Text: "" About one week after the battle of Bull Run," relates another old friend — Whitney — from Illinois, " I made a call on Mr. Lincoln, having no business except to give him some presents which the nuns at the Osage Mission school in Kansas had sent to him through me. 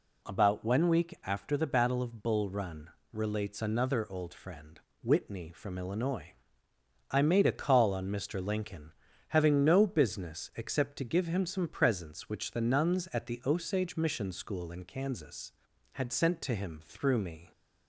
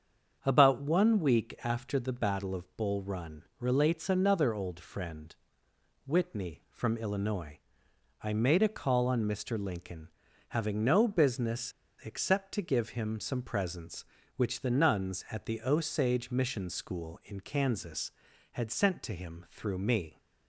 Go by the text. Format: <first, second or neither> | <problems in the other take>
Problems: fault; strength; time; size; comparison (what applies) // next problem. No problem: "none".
first | starts louder than the rest; strong; until 1.4 s; 7 dB // pauses between "business" and "except"; slight; at 11.7 s; 0.31 s long